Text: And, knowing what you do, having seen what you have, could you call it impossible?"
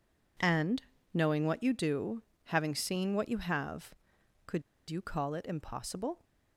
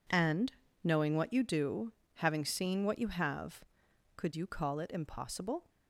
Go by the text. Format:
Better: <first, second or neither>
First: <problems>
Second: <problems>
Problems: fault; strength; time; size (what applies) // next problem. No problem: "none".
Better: second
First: pauses between "could" and "you"; slight; at 4.6 s; 0.27 s long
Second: none